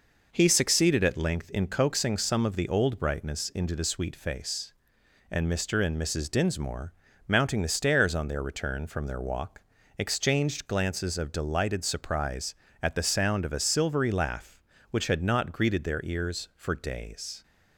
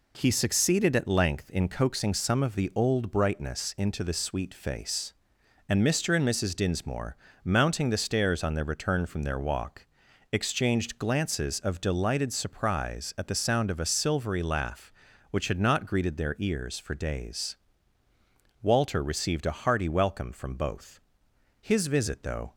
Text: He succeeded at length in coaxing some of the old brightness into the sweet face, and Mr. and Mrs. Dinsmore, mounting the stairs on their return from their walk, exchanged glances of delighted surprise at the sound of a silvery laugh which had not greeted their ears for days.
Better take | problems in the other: first | goes on to say "Walter received a hearty welcome from both His visit though"; strong; from 18.6 s on; 3.9 s long

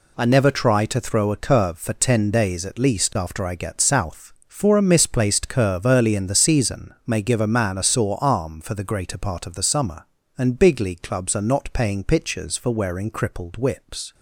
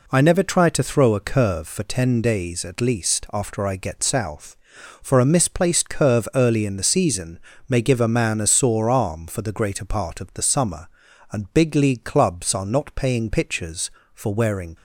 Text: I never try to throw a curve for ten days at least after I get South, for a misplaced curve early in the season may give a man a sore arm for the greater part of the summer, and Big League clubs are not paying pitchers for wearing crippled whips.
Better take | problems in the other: first | pauses between "season" and "may"; slight; at 7.3 s; 0.28 s long // stops before "crippled whips"; at 14.7 s

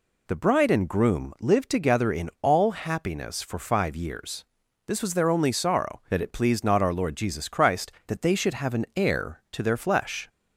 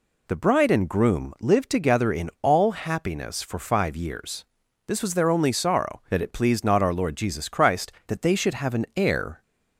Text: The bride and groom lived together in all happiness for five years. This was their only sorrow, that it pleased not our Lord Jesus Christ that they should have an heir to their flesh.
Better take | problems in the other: first | stops before "to their flesh"; at 9.4 s

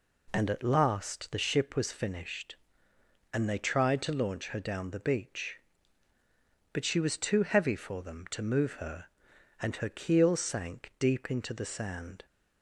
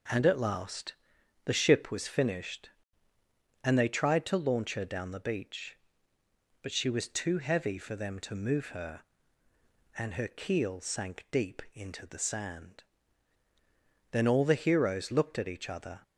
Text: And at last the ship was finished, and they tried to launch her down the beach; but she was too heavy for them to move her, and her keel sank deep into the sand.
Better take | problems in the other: first | pauses between "last" and "the"; noticeable; at 0.9 s; 0.50 s long // goes on to say "Then all the heroes looked at each other"; strong; from 14.1 s on; 1.9 s long

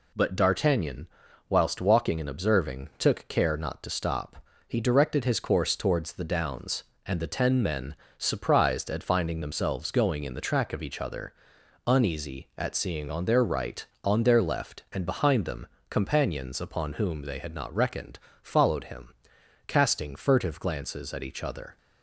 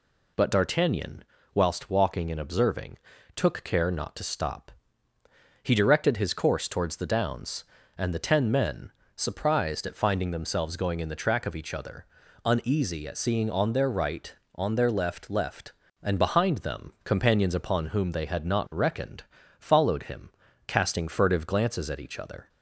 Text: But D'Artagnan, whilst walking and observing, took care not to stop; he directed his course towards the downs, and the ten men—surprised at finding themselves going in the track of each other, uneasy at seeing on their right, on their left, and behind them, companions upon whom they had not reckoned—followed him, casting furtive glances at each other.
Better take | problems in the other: first | says "left" twice; at 15.2 s

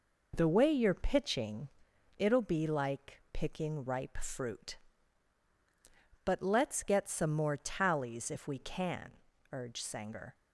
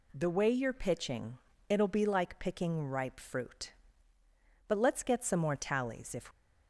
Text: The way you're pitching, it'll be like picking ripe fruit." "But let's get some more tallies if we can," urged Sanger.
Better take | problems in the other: first | stops before "we can urged Sanger"; at 6.3 s

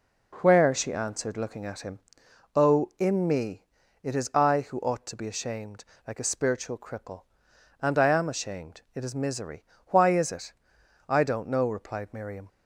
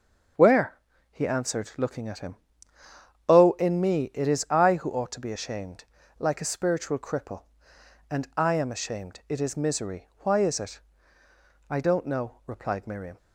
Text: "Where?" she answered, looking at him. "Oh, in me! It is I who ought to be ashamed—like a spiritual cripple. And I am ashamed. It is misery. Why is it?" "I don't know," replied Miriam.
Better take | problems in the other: first | starts louder than the rest; until 1.7 s; 6.5 dB // says "he" for "she"; at 1.1 s

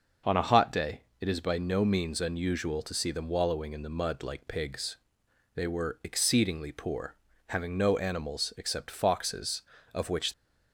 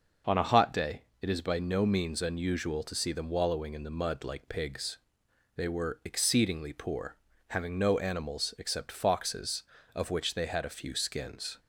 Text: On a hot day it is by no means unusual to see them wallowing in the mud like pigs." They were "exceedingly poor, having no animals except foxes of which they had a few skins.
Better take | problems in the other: second | starts louder than the rest; noticeable; until 1.4 s; 6 dB; noticeable in the second // pauses between "day" and "it"; slight; at 1.0 s; 0.18 s long; slight in the second // stops before "they had a few skins"; at 10.3 s

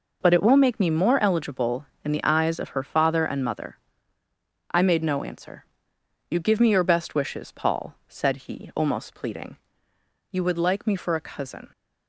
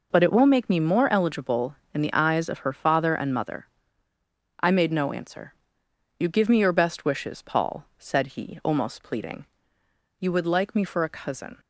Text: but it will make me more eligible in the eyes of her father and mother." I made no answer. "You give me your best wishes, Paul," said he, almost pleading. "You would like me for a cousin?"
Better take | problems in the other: neither | none

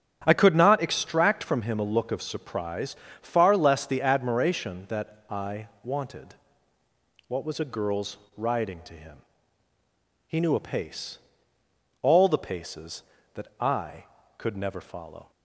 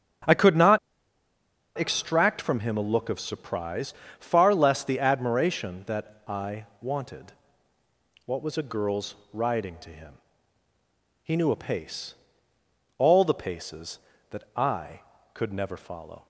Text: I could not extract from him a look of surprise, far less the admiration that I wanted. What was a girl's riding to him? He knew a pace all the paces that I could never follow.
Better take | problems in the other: first | starts louder than the rest; strong; until 2.2 s; 9 dB; strong in the first // pauses between "not" and "extract"; at 0.7 s; 0.99 s long // pauses between "I" and "wanted"; slight; at 6.6 s; 0.16 s long; slight in the first // pauses between "girl's" and "riding"; slight; at 9.1 s; 0.18 s long; slight in the first // pauses between "pace" and "all"; noticeable; at 12.1 s; 0.84 s long; noticeable in the first

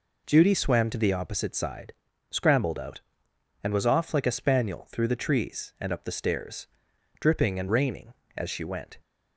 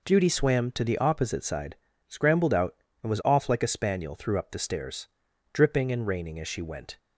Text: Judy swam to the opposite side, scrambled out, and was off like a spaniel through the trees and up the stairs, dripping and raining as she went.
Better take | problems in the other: first | skips "the trees and"; at 4.3 s

